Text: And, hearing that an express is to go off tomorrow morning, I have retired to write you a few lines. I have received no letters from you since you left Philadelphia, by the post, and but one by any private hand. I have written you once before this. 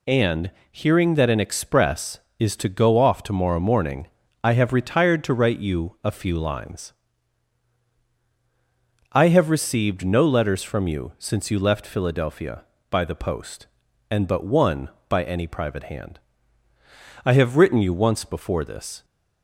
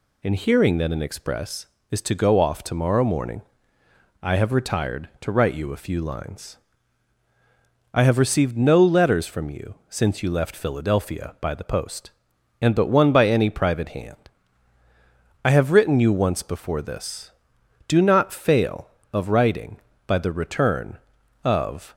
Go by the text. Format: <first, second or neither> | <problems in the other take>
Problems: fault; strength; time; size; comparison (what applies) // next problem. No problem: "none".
first | goes on to say "Do not fail of writing by the return of"; strong; from 17.8 s on; 4.0 s long